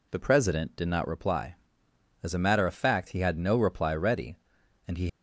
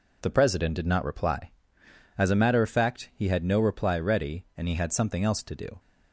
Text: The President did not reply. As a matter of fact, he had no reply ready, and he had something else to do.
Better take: second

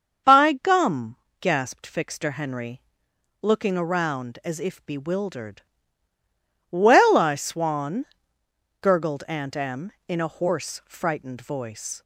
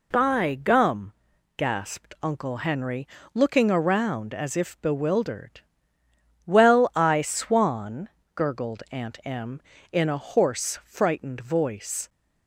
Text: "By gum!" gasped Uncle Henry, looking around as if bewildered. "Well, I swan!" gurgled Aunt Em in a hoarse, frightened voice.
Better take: second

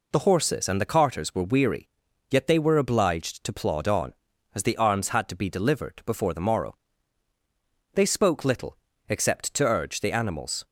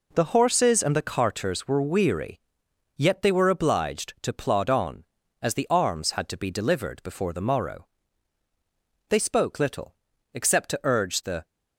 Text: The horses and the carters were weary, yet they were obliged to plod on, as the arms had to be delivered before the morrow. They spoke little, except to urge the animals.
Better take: first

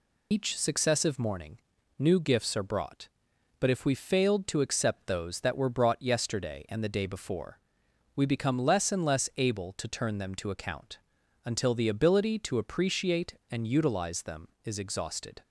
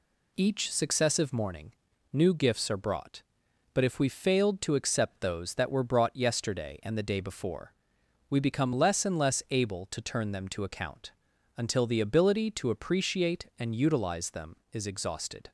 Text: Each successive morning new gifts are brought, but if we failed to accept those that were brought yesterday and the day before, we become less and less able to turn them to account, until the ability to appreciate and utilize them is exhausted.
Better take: second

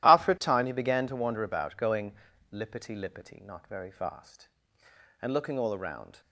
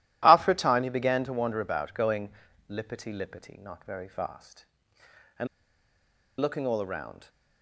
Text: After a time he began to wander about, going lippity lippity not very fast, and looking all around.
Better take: first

